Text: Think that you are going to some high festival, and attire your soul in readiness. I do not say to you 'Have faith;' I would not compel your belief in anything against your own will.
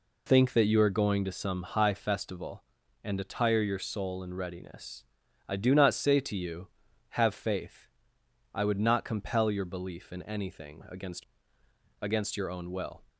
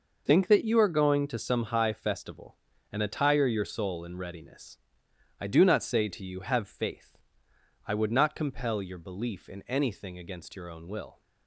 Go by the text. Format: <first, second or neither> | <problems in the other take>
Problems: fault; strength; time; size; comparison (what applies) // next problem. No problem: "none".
second | says "against" twice; at 12.0 s